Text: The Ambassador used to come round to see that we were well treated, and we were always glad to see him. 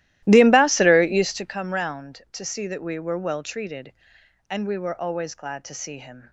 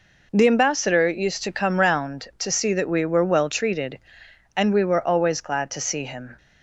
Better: second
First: starts louder than the rest; strong; until 1.5 s; 15.5 dB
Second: none

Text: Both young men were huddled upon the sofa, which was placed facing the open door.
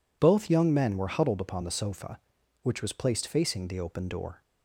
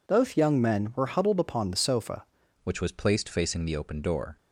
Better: first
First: none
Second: changes voice at "which"; from 2.6 s on; 1.7 s long

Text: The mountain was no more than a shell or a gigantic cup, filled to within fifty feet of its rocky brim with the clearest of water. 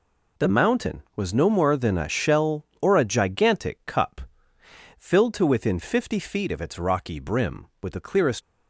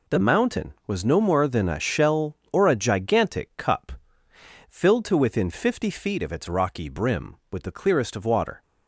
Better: second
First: stops before "of water"; at 8.4 s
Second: none

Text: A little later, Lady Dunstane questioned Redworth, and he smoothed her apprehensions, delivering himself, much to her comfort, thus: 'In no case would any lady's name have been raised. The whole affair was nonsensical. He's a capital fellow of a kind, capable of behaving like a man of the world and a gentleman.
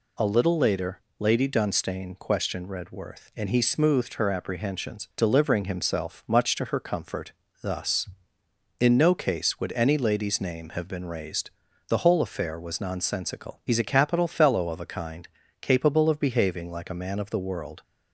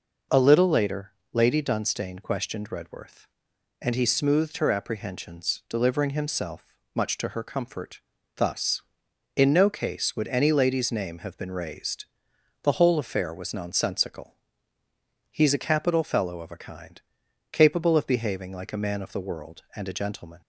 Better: second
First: stops before "and a gentleman"; at 17.8 s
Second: none

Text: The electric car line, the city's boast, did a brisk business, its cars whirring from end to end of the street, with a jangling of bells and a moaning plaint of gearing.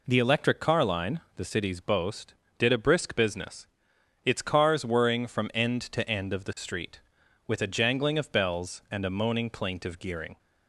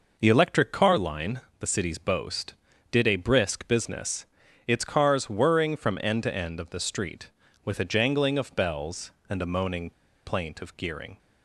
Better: first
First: none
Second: pauses between "moaning" and "plaint"; slight; at 9.9 s; 0.35 s long

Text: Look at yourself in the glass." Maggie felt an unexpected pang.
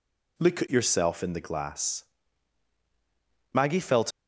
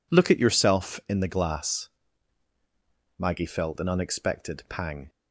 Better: second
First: stops before "an unexpected pang"; at 4.1 s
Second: none

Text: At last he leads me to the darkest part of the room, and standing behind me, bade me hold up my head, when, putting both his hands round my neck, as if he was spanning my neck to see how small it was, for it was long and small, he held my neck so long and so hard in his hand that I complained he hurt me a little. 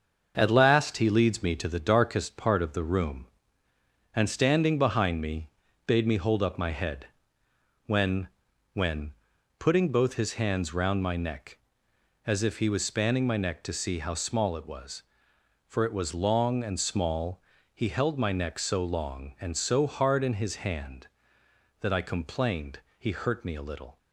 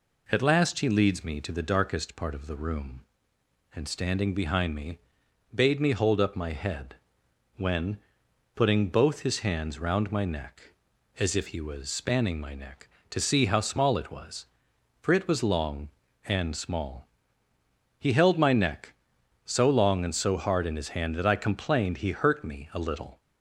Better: second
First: starts louder than the rest; until 1.3 s; 6.5 dB // says "when" twice; at 8.7 s // pauses between "complained" and "he"; slight; at 22.7 s; 0.18 s long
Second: none

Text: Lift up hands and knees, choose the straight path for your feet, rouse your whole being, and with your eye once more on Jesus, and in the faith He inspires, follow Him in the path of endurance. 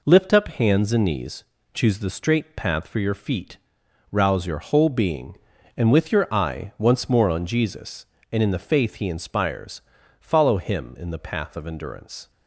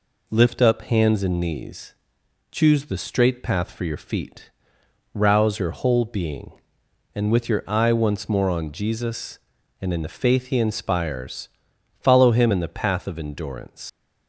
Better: first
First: none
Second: leaves "endurance" unfinished; at 13.8 s; 110 ms

